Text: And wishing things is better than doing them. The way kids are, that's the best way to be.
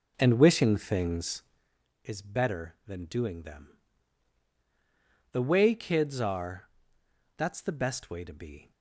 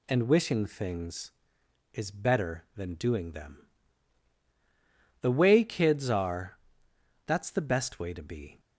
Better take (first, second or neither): second